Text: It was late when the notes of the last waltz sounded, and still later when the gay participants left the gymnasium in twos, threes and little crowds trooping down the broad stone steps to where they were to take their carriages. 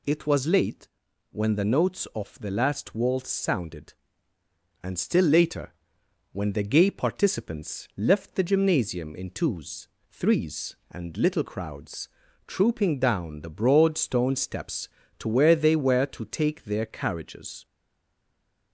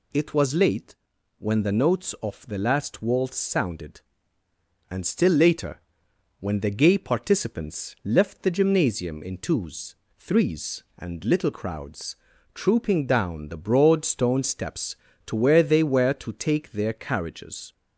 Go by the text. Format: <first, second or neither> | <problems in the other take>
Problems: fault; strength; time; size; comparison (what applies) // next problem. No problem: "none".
second | pauses between "late" and "when"; at 0.8 s; 0.44 s long; also in the second // pauses between "later" and "when"; noticeable; at 5.7 s; 0.58 s long; noticeable in the second // pauses between "crowds" and "trooping"; at 12.0 s; 0.40 s long; also in the second // stays silent after the last word; from 17.6 s on; 1.1 s long